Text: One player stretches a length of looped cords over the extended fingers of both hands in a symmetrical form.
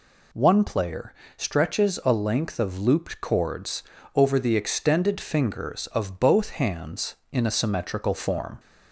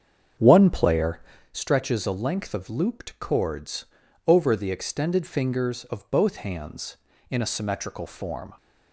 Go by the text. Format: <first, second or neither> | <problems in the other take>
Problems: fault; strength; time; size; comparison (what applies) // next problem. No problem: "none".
first | starts louder than the rest; strong; until 1.5 s; 7.5 dB // pauses between "player" and "stretches"; slight; at 1.1 s; 0.32 s long; slight in the first // pauses between "cords" and "over"; at 3.8 s; 0.42 s long; slight in the first